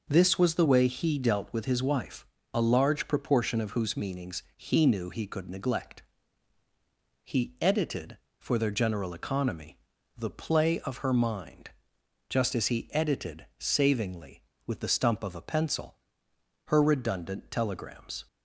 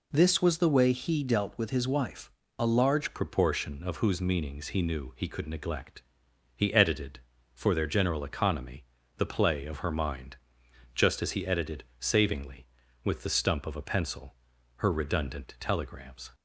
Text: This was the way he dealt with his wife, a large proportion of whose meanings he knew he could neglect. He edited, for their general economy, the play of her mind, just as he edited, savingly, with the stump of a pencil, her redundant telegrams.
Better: first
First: none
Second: changes voice at "proportion"; from 3.1 s on; 13.2 s long

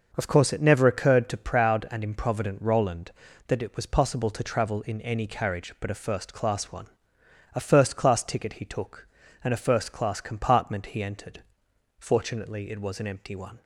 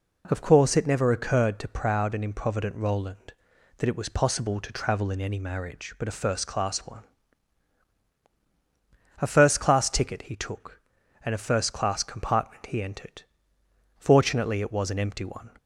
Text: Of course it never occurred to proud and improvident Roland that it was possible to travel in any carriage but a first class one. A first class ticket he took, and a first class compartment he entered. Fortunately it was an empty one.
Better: first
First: none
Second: says "marriage" for "carriage"; at 5.3 s

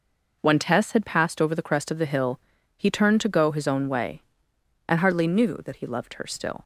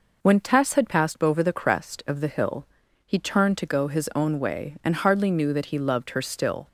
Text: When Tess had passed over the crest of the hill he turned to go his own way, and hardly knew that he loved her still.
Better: neither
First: pauses between "hill" and "he"; at 2.3 s; 0.38 s long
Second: pauses between "hill" and "he"; at 2.6 s; 0.42 s long

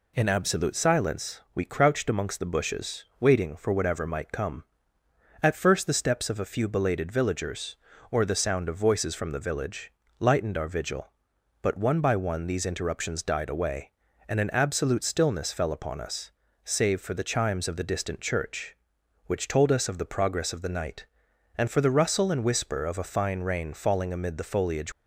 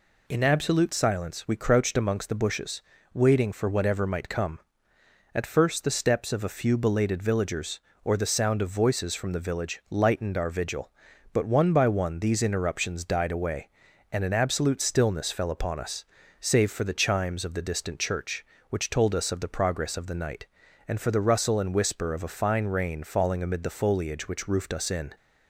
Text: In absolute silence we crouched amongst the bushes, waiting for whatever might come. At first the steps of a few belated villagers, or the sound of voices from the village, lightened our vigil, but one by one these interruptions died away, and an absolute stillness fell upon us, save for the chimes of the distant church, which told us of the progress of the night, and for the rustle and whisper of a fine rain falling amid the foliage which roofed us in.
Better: second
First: stops before "which roofed us in"; at 24.9 s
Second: none

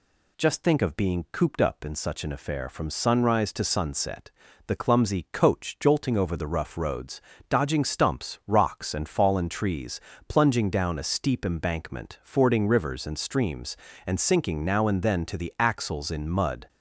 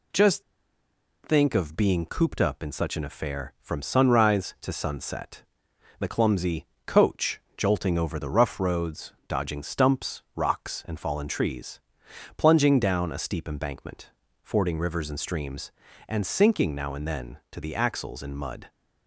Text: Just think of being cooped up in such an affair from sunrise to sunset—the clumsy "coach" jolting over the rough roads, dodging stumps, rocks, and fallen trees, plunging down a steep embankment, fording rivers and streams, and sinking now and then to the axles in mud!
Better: first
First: none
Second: pauses between "Just" and "think"; noticeable; at 0.4 s; 0.81 s long // pauses between "clumsy" and "coach"; slight; at 6.6 s; 0.20 s long // pauses between "coach" and "jolting"; slight; at 7.3 s; 0.18 s long

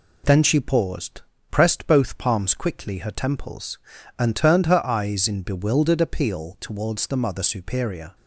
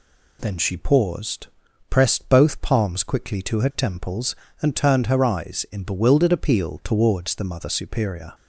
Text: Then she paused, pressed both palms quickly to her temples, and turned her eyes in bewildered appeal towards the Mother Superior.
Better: second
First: skips "to"; at 2.9 s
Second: none

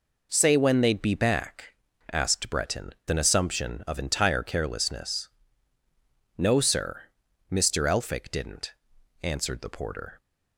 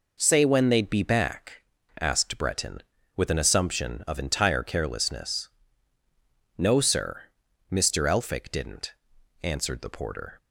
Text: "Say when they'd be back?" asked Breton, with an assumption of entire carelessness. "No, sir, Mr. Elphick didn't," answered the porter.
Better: second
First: skips "with"; at 3.0 s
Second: none

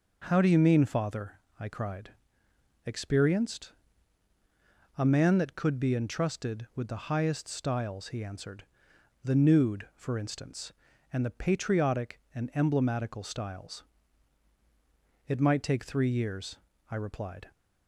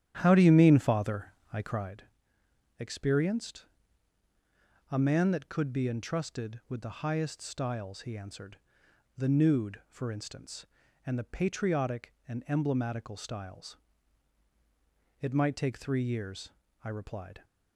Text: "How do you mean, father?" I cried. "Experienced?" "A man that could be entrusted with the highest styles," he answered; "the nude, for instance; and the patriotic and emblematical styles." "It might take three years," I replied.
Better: first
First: none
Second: starts louder than the rest; strong; until 2.0 s; 11 dB

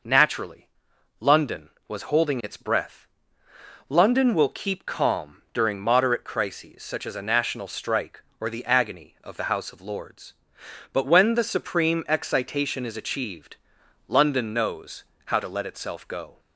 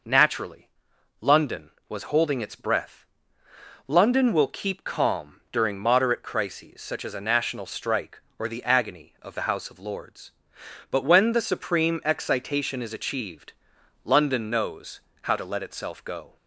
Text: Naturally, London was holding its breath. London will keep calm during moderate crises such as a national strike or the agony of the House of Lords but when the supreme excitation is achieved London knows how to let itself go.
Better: neither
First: pauses between "achieved" and "London"; noticeable; at 13.5 s; 0.52 s long // pauses between "knows" and "how"; slight; at 15.0 s; 0.22 s long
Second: pauses between "achieved" and "London"; noticeable; at 13.5 s; 0.52 s long // pauses between "knows" and "how"; slight; at 14.9 s; 0.22 s long

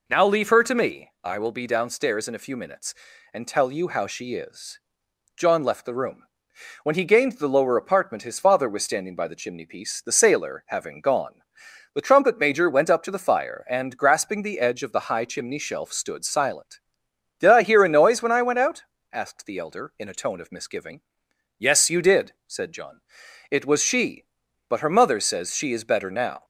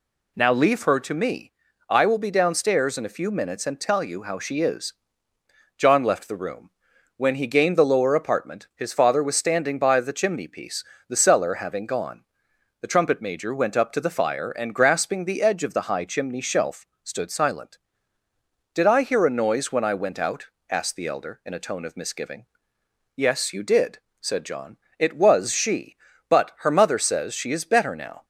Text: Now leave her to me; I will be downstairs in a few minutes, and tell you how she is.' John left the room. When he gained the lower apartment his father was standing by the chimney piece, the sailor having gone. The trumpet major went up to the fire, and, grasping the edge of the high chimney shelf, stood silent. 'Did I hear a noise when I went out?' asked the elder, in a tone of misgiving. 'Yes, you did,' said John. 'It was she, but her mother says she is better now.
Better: first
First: none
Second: says "cellar" for "sailor"; at 11.1 s

